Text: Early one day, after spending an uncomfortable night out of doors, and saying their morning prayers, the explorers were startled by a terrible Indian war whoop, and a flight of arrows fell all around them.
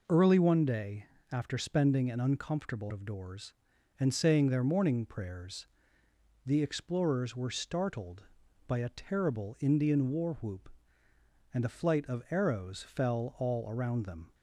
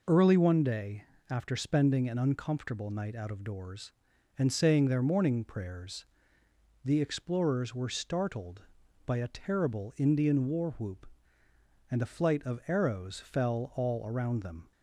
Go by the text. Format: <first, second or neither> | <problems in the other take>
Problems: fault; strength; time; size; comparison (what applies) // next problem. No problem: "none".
second | skips "night out"; at 2.9 s